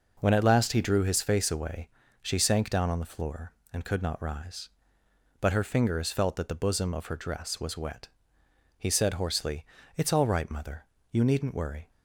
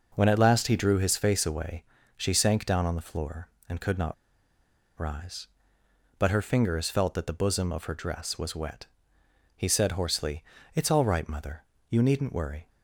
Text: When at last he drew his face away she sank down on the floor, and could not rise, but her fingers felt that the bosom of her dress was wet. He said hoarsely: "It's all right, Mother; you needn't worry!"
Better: first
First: pauses between "away" and "she"; slight; at 1.8 s; 0.34 s long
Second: pauses between "away" and "she"; slight; at 1.8 s; 0.34 s long // pauses between "not" and "rise"; noticeable; at 4.1 s; 0.84 s long

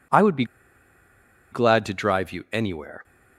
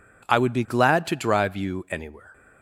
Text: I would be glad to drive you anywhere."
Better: second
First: pauses between "be" and "glad"; at 0.4 s; 1.0 s long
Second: none

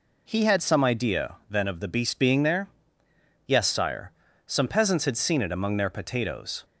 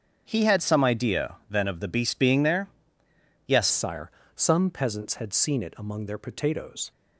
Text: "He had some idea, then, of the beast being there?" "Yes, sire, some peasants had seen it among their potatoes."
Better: first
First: none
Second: starts louder than the rest; strong; until 1.2 s; 7 dB // changes voice at "sire"; from 3.7 s on; 3.2 s long

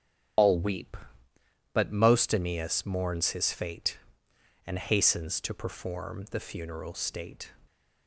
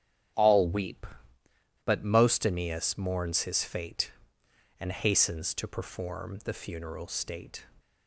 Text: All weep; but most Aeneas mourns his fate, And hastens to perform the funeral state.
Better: second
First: loses the start of "All"; at 0.3 s; 120 ms // starts louder than the rest; strong; until 2.1 s; 9.5 dB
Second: starts louder than the rest; strong; until 2.1 s; 9.5 dB

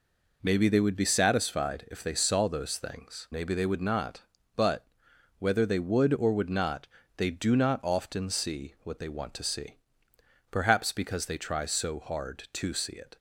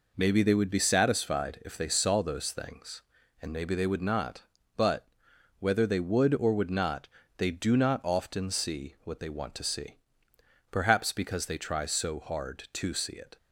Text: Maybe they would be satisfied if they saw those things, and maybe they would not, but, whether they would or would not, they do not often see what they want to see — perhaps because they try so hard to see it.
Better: second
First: skips "and"; at 3.2 s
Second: none

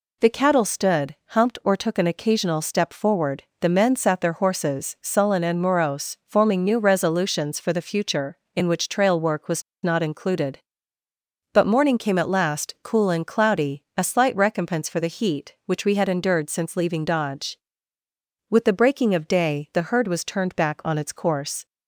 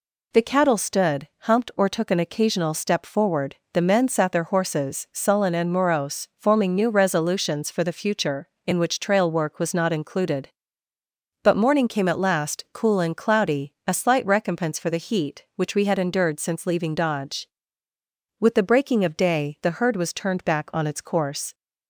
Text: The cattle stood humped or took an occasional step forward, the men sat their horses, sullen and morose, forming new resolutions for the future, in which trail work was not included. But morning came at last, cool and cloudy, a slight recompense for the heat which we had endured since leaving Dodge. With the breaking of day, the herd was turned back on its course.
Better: second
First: pauses between "stood" and "humped"; slight; at 1.1 s; 0.16 s long // pauses between "was" and "not"; slight; at 9.6 s; 0.21 s long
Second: pauses between "stood" and "humped"; slight; at 1.2 s; 0.16 s long

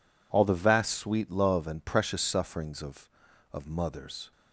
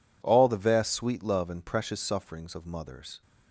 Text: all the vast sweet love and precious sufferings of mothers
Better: second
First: says "of" twice; at 3.5 s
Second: none

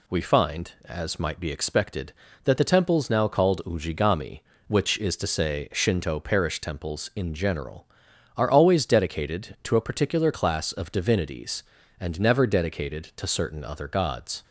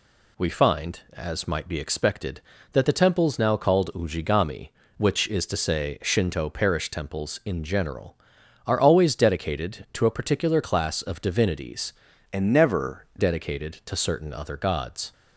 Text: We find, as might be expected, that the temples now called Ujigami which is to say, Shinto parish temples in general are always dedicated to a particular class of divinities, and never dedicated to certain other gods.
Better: first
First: none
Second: changes voice from "and" to "never"; from 12.3 to 13.0 s; 0.7 s long

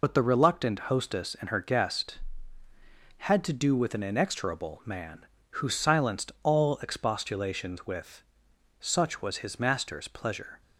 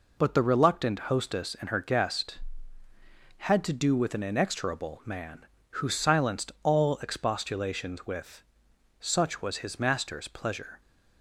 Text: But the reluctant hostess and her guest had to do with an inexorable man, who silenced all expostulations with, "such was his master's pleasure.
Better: second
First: loses the start of "But"; at 0.0 s; 45 ms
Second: none

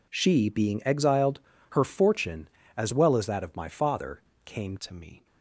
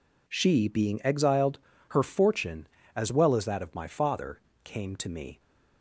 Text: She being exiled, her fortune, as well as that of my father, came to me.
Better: second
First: changes voice at "to"; from 4.7 s on; 0.5 s long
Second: none

